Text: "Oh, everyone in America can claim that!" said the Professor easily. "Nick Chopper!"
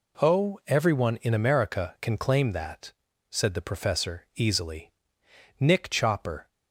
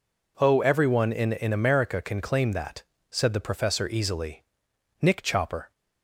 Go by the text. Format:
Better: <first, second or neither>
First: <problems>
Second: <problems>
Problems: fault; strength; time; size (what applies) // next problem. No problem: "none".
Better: first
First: none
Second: says "in" twice; at 1.3 s